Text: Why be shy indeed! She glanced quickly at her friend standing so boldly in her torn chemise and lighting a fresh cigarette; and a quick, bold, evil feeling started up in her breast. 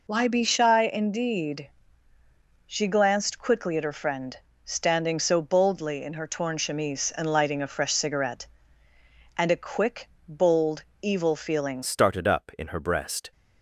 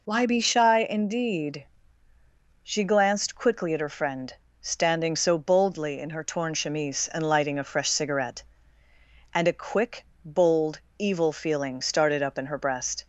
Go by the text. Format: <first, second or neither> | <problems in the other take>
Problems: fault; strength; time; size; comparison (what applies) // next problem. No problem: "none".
second | pauses between "friend" and "standing"; slight; at 4.3 s; 0.26 s long; slight in the second // changes voice at "started"; from 11.8 s on; 1.5 s long